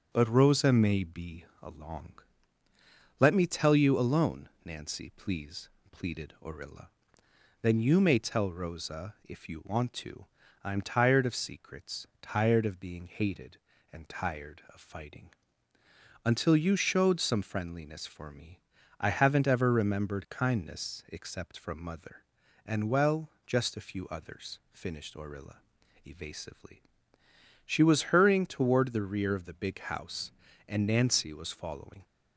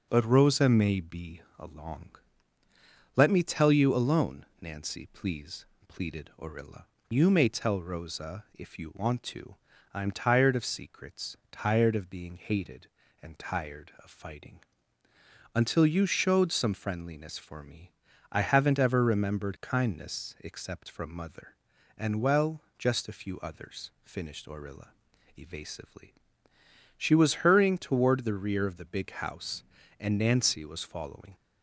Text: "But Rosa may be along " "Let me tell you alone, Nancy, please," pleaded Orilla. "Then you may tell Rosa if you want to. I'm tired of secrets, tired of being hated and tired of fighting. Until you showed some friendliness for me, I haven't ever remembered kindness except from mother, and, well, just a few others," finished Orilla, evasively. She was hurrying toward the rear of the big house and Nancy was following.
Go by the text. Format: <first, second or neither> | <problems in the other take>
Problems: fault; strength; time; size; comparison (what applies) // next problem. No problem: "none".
first | starts louder than the rest; until 1.1 s; 6.5 dB // pauses between "be" and "along"; slight; at 1.4 s; 0.18 s long; slight in the first // skips "Then"; at 6.9 s